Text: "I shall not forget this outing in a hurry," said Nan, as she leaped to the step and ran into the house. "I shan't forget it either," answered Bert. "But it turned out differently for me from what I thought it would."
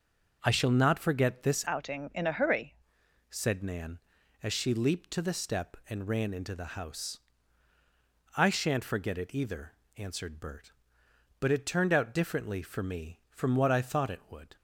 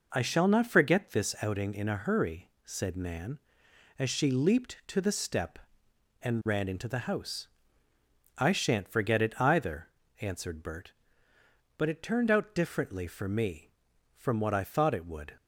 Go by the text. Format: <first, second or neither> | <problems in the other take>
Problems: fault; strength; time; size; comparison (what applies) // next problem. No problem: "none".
second | changes voice from "outing" to "hurry"; from 1.6 to 2.7 s; 1.1 s long